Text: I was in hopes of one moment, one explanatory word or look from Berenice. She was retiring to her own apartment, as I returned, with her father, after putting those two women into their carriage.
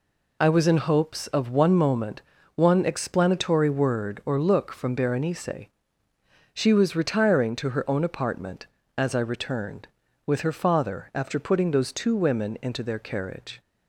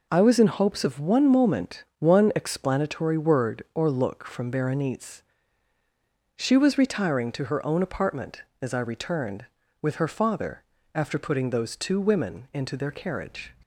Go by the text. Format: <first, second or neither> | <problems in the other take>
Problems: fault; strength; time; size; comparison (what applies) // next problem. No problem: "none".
neither | none